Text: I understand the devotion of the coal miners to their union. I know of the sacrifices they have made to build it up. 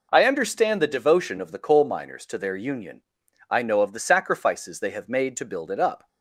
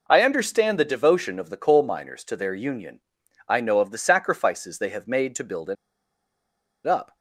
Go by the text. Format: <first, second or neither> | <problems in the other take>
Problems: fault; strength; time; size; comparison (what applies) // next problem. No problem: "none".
first | pauses between "it" and "up"; at 5.7 s; 1.1 s long